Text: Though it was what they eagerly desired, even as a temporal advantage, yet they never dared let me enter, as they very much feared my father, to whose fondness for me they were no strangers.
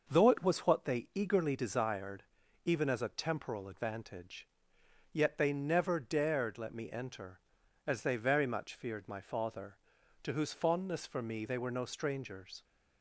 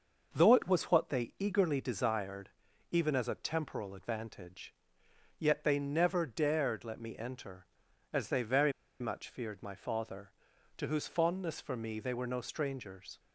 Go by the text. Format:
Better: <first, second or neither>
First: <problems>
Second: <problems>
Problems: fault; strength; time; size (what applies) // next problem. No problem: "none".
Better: first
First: starts louder than the rest; noticeable; until 1.0 s; 6 dB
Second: starts louder than the rest; noticeable; until 1.3 s; 6 dB // pauses between "very" and "much"; slight; at 8.7 s; 0.29 s long